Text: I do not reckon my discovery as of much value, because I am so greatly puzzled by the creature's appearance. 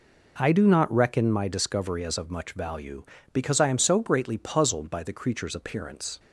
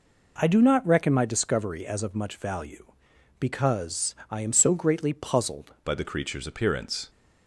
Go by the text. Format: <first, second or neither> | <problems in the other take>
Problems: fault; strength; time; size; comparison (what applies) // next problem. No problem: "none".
first | changes voice at "by"; from 5.8 s on; 1.2 s long